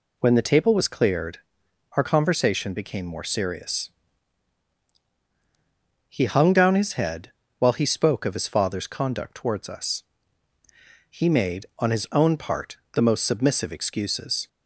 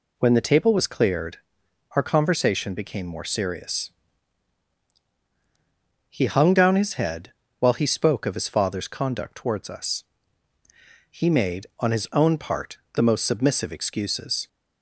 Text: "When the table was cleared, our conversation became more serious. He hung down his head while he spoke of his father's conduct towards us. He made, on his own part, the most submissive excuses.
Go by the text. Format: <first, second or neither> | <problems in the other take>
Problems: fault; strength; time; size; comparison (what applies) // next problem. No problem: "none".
neither | pauses between "head" and "while"; slight; the same in both